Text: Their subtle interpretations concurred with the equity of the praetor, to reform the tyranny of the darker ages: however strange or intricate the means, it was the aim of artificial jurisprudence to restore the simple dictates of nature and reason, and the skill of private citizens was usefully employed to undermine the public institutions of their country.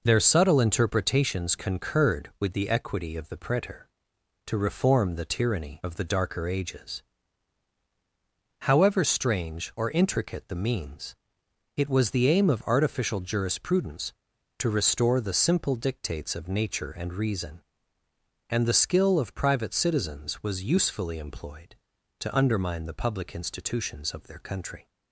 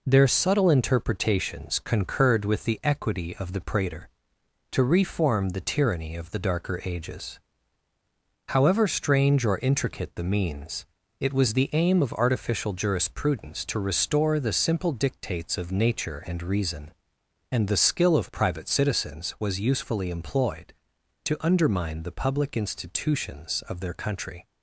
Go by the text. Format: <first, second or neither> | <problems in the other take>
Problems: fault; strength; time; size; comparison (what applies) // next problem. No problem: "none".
neither | none